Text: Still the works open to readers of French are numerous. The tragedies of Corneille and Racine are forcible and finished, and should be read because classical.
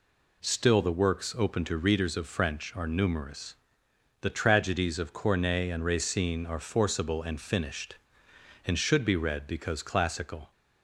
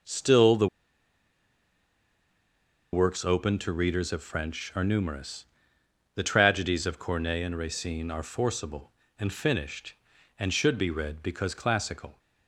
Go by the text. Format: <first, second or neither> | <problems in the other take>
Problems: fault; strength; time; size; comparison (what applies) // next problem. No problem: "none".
first | pauses between "the" and "works"; strong; at 0.6 s; 2.2 s long